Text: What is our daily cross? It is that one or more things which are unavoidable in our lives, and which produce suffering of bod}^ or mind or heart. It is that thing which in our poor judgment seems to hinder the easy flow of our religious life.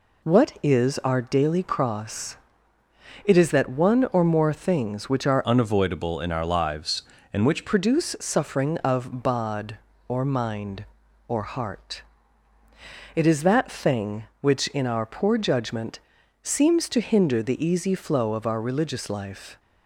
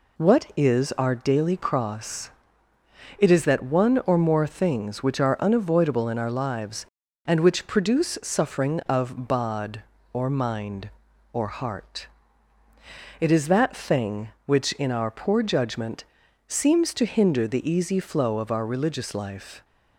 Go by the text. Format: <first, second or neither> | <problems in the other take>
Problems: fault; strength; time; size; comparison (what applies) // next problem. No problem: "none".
second | changes voice from "unavoidable" to "which"; from 5.4 to 7.6 s; 2.2 s long // pauses between "judgment" and "seems"; at 15.9 s; 0.42 s long; also in the second